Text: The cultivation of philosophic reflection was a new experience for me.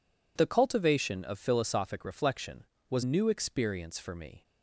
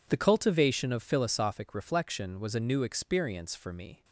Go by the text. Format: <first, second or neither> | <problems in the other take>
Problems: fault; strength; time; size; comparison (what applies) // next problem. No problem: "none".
second | skips "a"; at 3.0 s